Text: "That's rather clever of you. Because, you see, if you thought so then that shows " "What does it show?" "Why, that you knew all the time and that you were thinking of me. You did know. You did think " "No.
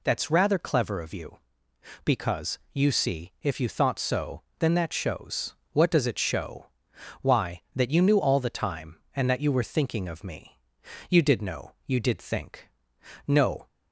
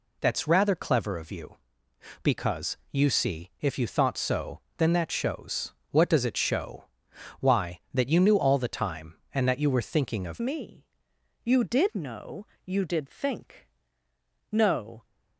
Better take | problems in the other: first | pauses between "so" and "then"; slight; at 4.6 s; 0.18 s long; slight in the first // changes voice at "me"; from 10.4 s on; 4.6 s long

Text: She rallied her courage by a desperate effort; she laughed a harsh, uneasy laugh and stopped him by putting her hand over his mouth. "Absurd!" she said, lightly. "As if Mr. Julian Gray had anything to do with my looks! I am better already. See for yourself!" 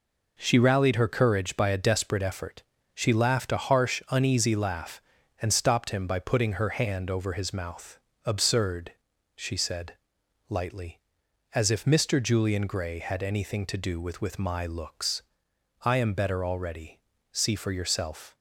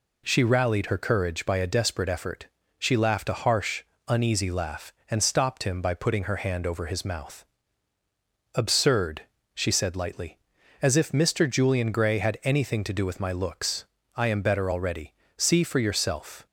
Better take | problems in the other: second | says "with" twice; at 14.2 s

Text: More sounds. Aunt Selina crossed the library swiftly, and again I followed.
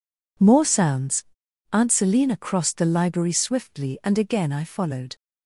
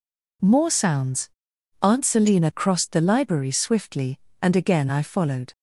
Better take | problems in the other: neither | none

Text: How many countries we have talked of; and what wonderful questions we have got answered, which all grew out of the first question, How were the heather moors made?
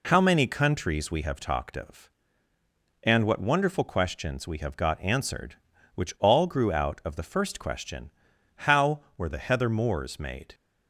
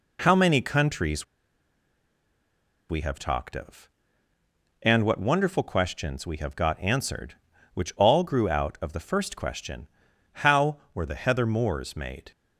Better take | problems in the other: first | pauses between "countries" and "we"; strong; at 1.2 s; 1.6 s long

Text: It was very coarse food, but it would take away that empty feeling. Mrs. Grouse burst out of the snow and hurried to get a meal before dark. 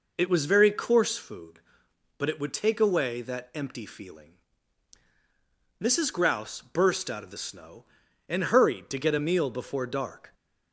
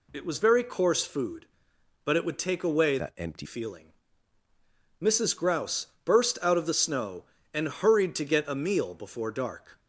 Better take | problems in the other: first | changes voice from "that" to "empty"; from 2.9 to 3.4 s; 0.5 s long // pauses between "Grouse" and "burst"; slight; at 5.8 s; 0.18 s long

